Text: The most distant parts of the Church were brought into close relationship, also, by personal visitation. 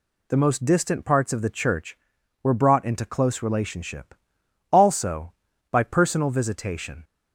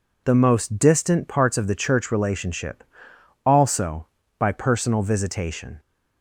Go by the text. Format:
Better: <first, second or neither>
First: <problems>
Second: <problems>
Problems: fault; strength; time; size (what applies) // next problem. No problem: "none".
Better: first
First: none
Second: skips "were brought into close"; at 2.1 s